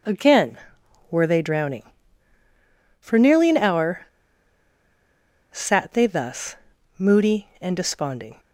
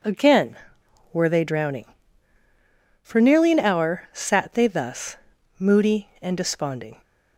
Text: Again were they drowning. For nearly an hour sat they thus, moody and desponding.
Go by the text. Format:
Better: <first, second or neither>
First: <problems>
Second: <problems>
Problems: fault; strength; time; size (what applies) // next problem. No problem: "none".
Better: second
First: pauses between "hour" and "sat"; strong; at 4.0 s; 1.4 s long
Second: none